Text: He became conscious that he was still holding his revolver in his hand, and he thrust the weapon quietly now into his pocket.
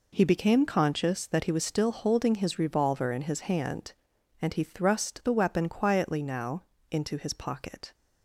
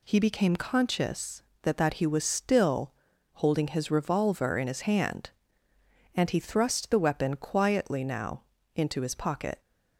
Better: first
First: pauses between "now" and "into"; slight; at 6.6 s; 0.28 s long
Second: says "that" twice; at 1.7 s // pauses between "still" and "holding"; at 2.9 s; 0.42 s long // pauses between "now" and "into"; slight; at 8.4 s; 0.32 s long

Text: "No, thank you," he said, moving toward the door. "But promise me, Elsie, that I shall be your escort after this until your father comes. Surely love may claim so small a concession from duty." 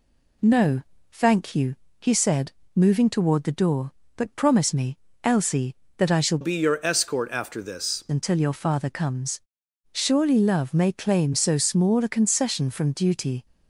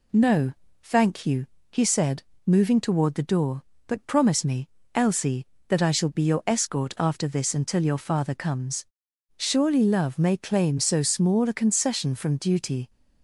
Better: second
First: changes voice from "be" to "this"; from 6.4 to 8.0 s; 1.6 s long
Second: none

